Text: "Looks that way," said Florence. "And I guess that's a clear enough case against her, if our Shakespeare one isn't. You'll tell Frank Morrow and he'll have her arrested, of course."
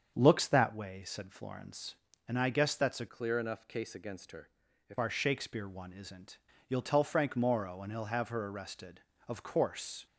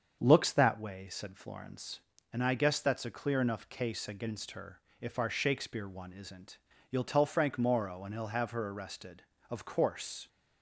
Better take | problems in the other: second | starts louder than the rest; strong; until 1.1 s; 7 dB; also in the second // changes voice from "clear" to "if"; from 3.0 to 4.9 s; 1.9 s long

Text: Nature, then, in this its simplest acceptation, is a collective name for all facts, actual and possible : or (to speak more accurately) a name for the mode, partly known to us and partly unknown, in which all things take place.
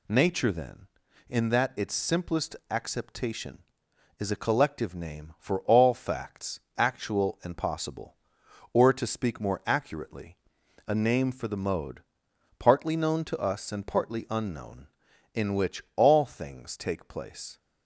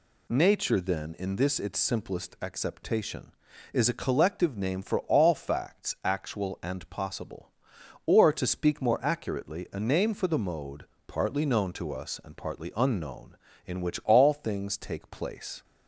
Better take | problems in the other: second | says "that" for "this"; at 1.4 s

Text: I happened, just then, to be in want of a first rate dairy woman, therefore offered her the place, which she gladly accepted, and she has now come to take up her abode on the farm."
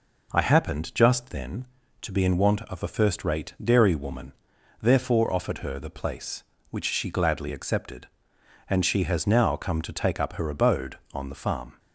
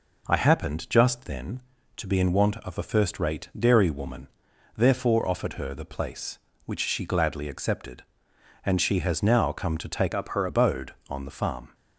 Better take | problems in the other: first | changes voice from "up" to "her"; from 10.1 to 10.4 s; 0.3 s long

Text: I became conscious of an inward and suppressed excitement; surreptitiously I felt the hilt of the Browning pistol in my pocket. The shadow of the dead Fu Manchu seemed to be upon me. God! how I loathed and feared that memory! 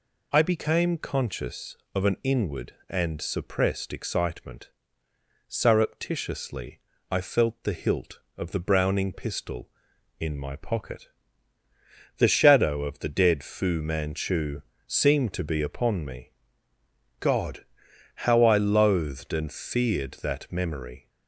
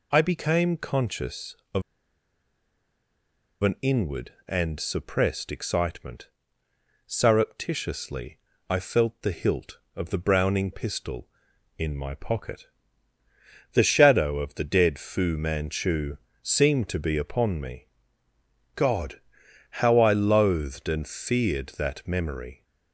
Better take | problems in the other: first | pauses between "of" and "an"; strong; at 1.8 s; 1.7 s long // pauses between "surreptitiously" and "I"; slight; at 8.3 s; 0.28 s long; slight in the first // pauses between "Manchu" and "seemed"; slight; at 16.1 s; 0.24 s long; slight in the first

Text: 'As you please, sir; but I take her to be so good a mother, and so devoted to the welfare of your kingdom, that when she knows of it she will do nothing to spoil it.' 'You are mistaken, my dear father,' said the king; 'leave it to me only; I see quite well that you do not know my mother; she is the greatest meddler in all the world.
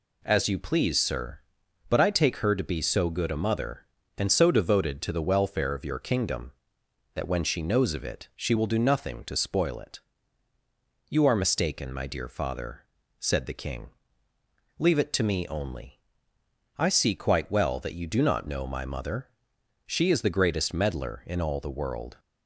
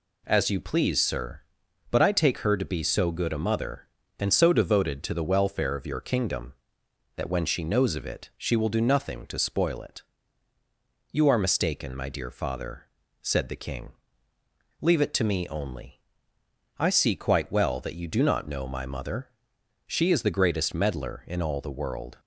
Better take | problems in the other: neither | none

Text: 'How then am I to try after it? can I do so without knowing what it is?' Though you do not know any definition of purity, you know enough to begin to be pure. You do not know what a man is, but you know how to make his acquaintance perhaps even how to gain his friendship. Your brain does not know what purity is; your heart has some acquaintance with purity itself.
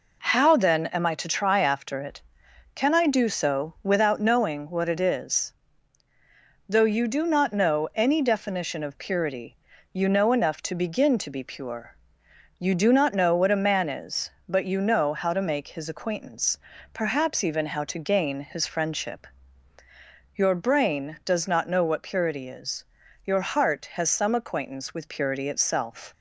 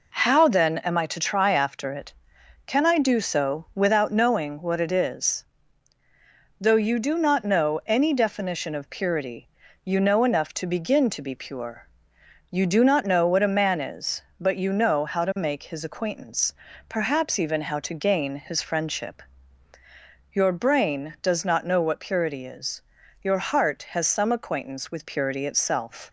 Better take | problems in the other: neither | pauses between "acquaintance" and "perhaps"; slight; the same in both

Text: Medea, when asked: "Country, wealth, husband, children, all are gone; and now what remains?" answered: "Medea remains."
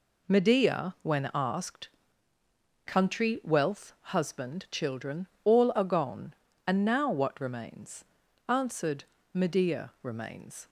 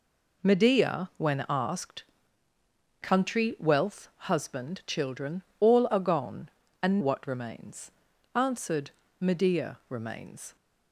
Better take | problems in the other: first | skips "now"; at 7.0 s

